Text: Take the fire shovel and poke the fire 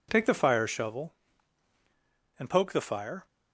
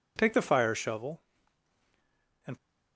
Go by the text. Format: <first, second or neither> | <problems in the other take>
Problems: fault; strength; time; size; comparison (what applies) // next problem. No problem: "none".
first | stops before "poke the fire"; at 2.5 s